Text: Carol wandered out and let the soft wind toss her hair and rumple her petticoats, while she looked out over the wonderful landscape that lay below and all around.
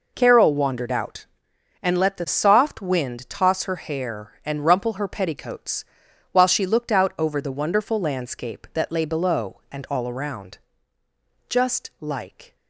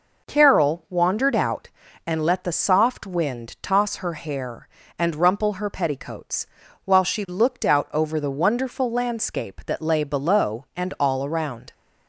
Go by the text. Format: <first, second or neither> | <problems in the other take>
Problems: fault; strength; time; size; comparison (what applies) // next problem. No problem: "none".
second | goes on to say "Just like"; noticeable; from 11.4 s on; 1.0 s long